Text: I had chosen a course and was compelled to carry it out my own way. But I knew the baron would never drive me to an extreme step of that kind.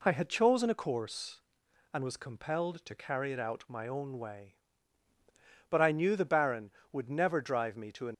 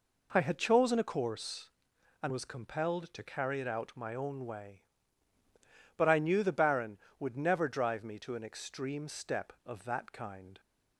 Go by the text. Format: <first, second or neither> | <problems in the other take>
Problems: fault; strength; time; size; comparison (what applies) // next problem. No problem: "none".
second | stops before "extreme step of that kind"; at 8.1 s